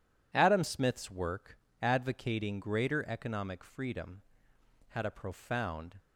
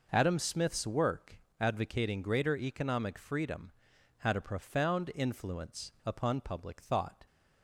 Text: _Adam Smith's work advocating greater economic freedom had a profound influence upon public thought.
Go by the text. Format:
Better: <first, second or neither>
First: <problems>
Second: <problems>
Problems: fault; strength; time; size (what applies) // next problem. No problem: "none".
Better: second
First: pauses between "work" and "advocating"; slight; at 1.5 s; 0.24 s long // stops before "influence upon public thought"; at 5.9 s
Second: pauses between "work" and "advocating"; slight; at 1.3 s; 0.22 s long